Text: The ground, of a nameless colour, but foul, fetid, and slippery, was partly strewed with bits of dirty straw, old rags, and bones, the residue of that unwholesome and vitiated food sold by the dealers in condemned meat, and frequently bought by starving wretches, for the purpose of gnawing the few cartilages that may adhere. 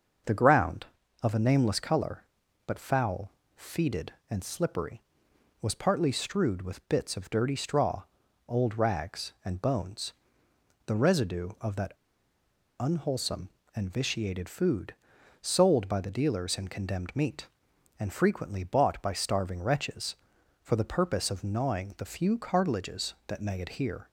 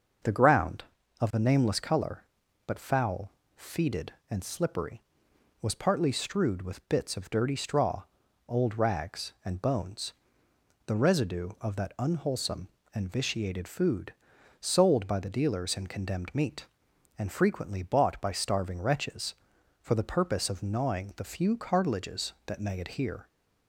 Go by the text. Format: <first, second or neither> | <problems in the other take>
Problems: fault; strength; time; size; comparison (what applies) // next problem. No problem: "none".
second | starts louder than the rest; until 1.5 s; 6 dB; also in the second // pauses between "that" and "unwholesome"; noticeable; at 11.9 s; 0.87 s long // pauses between "food" and "sold"; noticeable; at 14.9 s; 0.48 s long; noticeable in the second